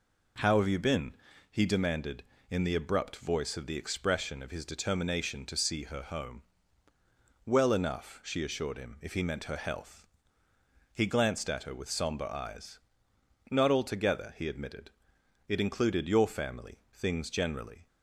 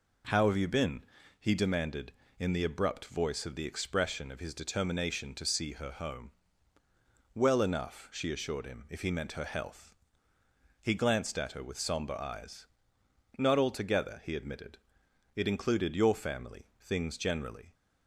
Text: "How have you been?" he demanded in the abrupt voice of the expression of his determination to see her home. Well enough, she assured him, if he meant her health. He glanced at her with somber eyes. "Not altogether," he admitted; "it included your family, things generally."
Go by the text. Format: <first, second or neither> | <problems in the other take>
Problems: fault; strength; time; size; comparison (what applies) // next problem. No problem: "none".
neither | none